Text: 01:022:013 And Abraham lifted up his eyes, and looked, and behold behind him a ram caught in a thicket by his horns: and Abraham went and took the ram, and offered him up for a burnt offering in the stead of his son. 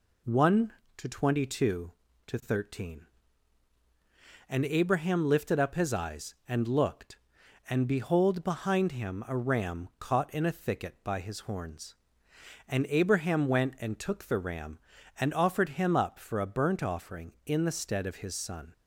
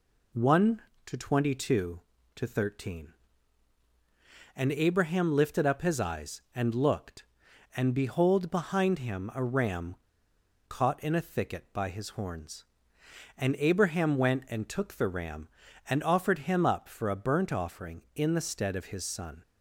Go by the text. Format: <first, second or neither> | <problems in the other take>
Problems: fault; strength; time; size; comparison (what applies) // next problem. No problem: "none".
first | pauses between "ram" and "caught"; noticeable; at 9.9 s; 0.76 s long